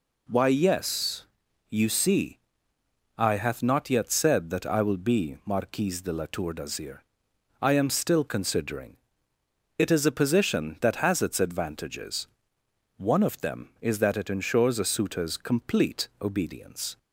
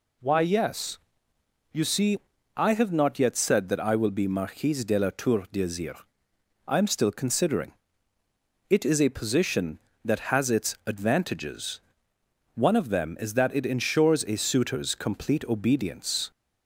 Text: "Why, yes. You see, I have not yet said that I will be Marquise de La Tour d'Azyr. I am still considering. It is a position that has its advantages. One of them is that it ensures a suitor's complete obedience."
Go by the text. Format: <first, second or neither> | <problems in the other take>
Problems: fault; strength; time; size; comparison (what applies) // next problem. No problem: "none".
second | says "hath" for "have"; at 3.3 s